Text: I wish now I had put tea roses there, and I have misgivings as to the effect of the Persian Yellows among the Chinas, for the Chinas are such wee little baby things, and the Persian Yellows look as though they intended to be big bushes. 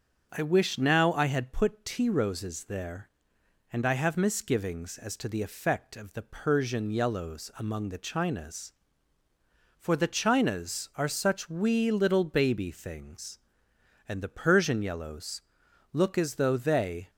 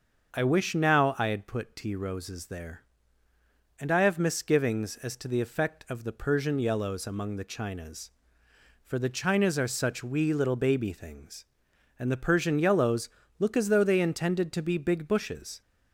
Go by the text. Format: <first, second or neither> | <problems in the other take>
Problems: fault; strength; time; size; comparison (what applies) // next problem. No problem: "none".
second | starts louder than the rest; until 1.3 s; 7 dB; also in the second // pauses between "Yellows" and "look"; noticeable; at 15.4 s; 0.50 s long; slight in the second // stops before "intended to be big bushes"; at 17.0 s